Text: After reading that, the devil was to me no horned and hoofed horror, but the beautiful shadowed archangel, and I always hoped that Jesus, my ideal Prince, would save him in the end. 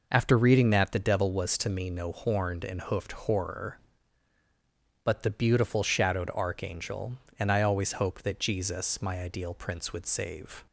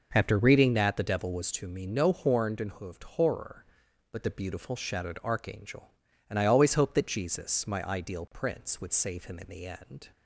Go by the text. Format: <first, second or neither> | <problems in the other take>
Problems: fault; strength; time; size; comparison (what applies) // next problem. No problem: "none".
second | stops before "him in the end"; at 10.6 s